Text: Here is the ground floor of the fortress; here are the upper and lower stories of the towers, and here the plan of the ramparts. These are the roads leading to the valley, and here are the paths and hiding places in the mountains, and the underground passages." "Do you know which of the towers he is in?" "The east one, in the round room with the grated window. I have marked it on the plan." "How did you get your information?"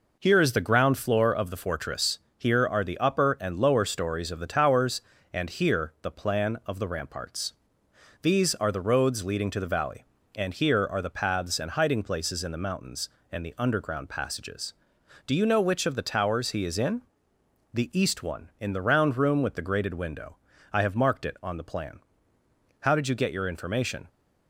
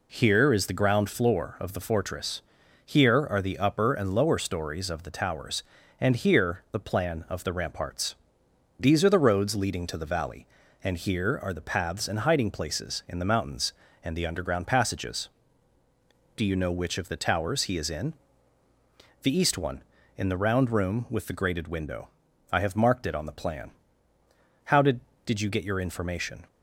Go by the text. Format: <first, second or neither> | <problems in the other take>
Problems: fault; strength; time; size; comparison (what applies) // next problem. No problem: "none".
first | says "did" twice; at 25.2 s